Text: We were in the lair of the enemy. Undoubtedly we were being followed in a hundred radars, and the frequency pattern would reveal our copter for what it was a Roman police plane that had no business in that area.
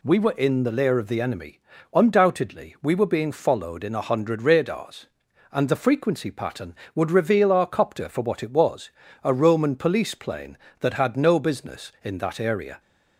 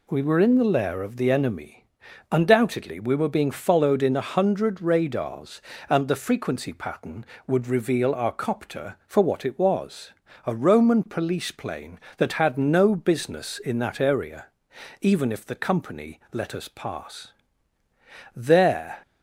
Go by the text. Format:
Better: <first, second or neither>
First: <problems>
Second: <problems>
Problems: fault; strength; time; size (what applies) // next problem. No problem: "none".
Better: first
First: pauses between "was" and "a"; slight; at 8.8 s; 0.34 s long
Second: pauses between "was" and "a"; slight; at 10.1 s; 0.34 s long // goes on to say "Even if the Company let us pass there"; strong; from 15.0 s on; 3.9 s long